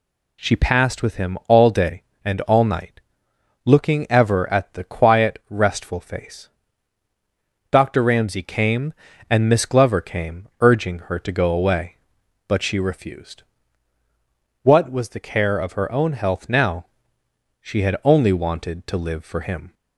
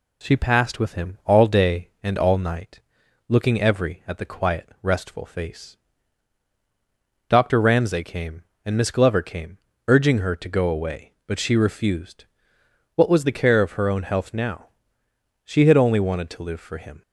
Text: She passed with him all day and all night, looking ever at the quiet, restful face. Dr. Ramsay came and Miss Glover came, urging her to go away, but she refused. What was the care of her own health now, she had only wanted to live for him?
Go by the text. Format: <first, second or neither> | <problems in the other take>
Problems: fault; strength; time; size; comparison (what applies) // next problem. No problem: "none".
first | says "every" for "ever"; at 3.5 s